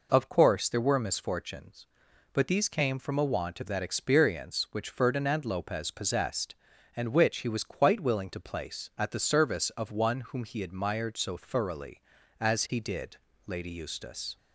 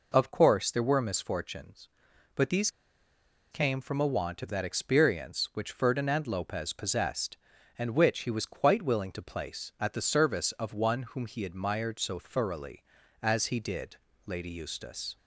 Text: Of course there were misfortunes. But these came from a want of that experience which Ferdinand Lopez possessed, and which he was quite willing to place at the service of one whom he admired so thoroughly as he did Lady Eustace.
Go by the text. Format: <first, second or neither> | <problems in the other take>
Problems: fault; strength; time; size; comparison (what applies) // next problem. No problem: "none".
first | pauses between "these" and "came"; noticeable; at 2.6 s; 0.82 s long // pauses between "did" and "Lady"; slight; at 13.9 s; 0.30 s long; slight in the first